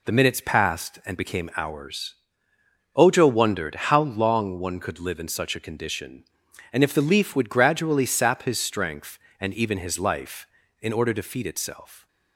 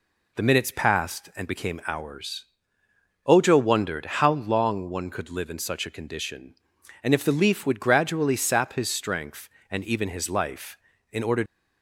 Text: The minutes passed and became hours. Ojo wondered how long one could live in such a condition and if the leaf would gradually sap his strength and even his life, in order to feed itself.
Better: first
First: none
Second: stops before "to feed itself"; at 11.4 s

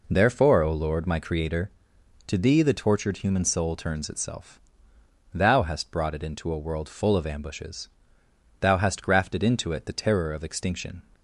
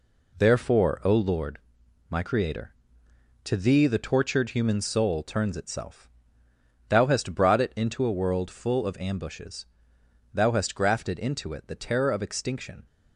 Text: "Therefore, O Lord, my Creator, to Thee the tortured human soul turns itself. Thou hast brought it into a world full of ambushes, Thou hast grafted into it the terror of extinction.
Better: neither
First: none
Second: none

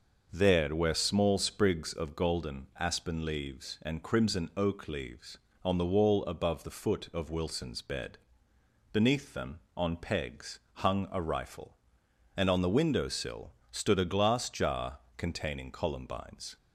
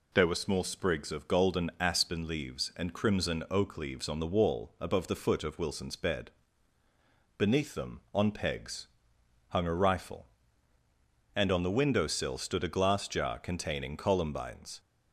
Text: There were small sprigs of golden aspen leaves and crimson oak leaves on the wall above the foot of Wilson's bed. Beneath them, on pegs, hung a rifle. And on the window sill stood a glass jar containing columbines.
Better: second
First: starts louder than the rest; noticeable; until 1.3 s; 6 dB // says "where" for "were"; at 0.7 s // pauses between "sill" and "stood"; slight; at 13.5 s; 0.18 s long // pauses between "jar" and "containing"; slight; at 14.9 s; 0.18 s long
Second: none

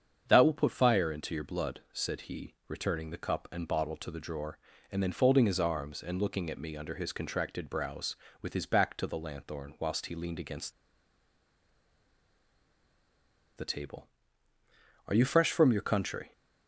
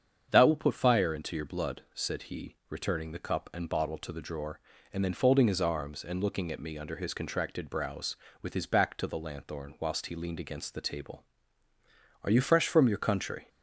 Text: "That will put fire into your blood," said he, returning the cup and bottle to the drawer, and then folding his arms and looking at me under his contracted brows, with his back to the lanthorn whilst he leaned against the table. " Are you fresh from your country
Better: second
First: starts louder than the rest; strong; until 1.2 s; 7.5 dB // pauses between "against" and "the"; strong; at 10.7 s; 2.8 s long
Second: starts louder than the rest; strong; until 1.3 s; 7.5 dB

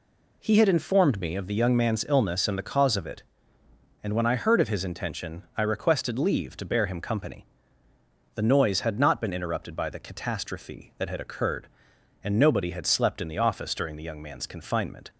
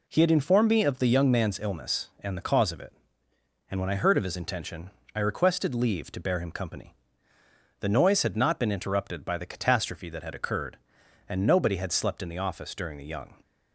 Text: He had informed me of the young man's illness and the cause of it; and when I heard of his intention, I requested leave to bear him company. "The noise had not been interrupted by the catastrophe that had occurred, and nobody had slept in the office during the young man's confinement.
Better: first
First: none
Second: stops before "man's confinement"; at 13.4 s

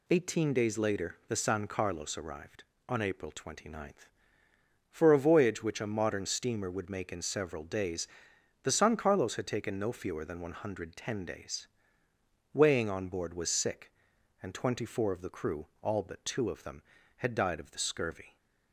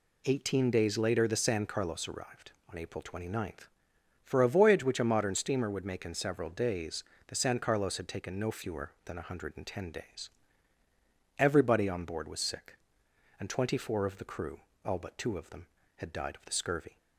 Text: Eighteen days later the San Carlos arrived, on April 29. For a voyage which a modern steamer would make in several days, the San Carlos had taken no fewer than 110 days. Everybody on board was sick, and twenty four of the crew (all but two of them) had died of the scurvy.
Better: second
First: says "Weighing" for "Everybody"; at 12.5 s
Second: none

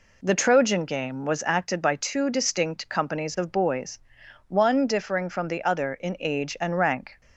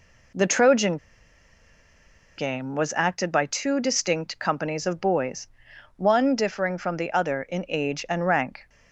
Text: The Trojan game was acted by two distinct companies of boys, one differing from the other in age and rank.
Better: first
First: none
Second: pauses between "Trojan" and "game"; strong; at 0.9 s; 1.4 s long

